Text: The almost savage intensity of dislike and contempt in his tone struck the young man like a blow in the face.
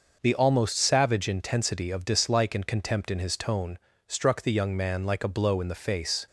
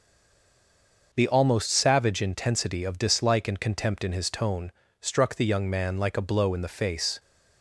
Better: first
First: pauses between "tone" and "struck"; slight; at 3.7 s; 0.30 s long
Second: stays silent before the first word; until 1.1 s; 1.1 s long // pauses between "tone" and "struck"; slight; at 4.7 s; 0.30 s long

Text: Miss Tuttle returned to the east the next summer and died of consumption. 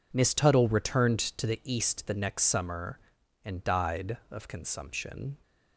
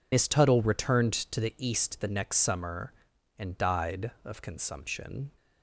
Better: first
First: none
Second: loses the start of "Miss"; at 0.1 s; 75 ms

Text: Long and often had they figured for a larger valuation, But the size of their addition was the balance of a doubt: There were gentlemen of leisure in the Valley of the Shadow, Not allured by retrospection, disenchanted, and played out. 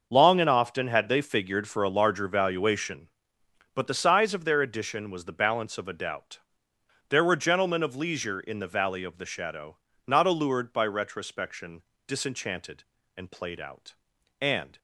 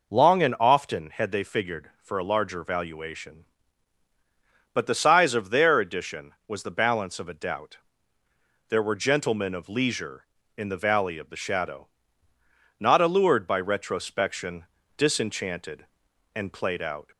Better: second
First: starts louder than the rest; until 1.1 s; 6 dB // goes on to say "And"; slight; from 14.3 s on; 0.38 s long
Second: none

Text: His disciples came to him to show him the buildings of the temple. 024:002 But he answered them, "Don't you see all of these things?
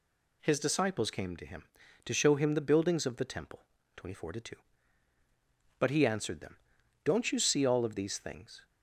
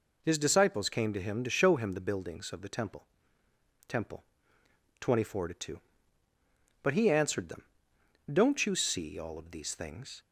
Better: first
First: none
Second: says "temple" twice; at 3.8 s

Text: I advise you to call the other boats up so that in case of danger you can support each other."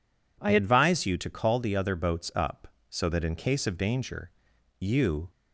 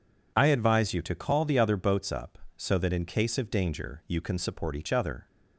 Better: second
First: pauses between "danger" and "you"; noticeable; at 4.3 s; 0.48 s long // stops before "can support each other"; at 5.2 s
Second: none

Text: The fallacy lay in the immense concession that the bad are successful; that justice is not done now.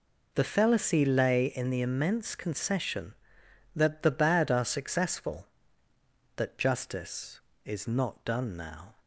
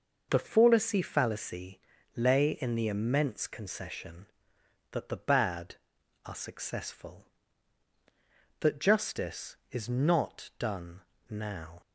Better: first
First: none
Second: says "fallacy" twice; at 1.0 s // pauses between "done" and "now"; slight; at 11.0 s; 0.30 s long

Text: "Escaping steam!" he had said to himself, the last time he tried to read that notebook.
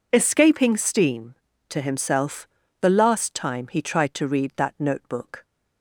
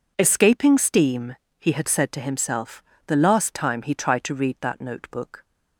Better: second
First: skips "he had said"; at 1.5 s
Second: none

